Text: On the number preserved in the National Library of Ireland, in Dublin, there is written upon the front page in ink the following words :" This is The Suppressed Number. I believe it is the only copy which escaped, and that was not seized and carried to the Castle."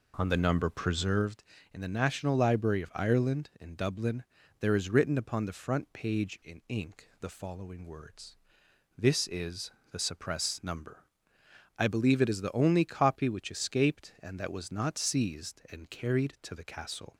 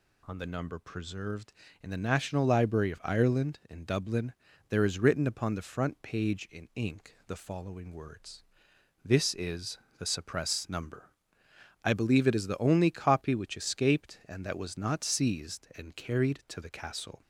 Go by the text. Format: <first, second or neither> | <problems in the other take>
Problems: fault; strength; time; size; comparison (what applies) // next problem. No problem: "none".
second | starts louder than the rest; until 1.4 s; 4 dB // pauses between "is" and "The"; slight; at 9.6 s; 0.22 s long; slight in the second